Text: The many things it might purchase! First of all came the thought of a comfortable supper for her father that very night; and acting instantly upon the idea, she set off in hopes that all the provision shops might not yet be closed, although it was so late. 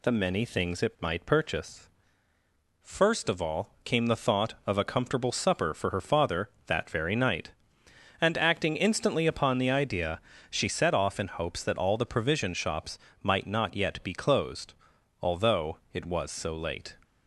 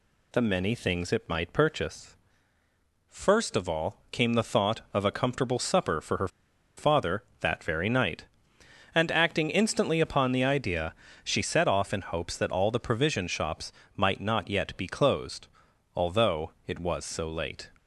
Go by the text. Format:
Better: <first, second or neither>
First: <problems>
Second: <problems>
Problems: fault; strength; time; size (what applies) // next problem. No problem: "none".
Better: first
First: pauses between "shops" and "might"; slight; at 12.9 s; 0.24 s long // pauses between "although" and "it"; slight; at 15.7 s; 0.16 s long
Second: pauses between "her" and "father"; noticeable; at 6.2 s; 0.49 s long // pauses between "shops" and "might"; slight; at 13.7 s; 0.24 s long // pauses between "although" and "it"; slight; at 16.5 s; 0.16 s long